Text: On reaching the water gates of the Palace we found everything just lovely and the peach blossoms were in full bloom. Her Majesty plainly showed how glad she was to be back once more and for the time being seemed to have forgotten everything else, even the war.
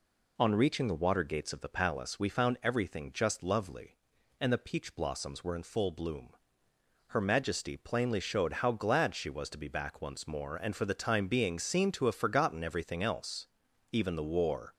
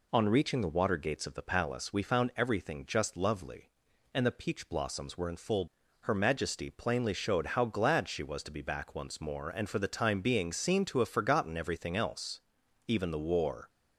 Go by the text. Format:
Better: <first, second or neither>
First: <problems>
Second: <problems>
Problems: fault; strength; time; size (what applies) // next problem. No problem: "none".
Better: first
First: none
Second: skips "bloom"; at 5.8 s